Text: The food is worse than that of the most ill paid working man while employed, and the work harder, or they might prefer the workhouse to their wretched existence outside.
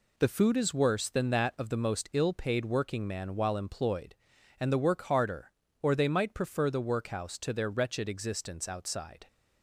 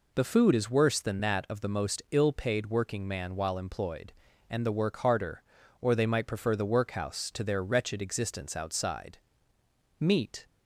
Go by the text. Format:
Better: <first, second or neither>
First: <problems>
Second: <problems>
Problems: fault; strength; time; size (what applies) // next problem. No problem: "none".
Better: first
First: none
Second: goes on to say "Meat"; slight; from 9.9 s on; 0.48 s long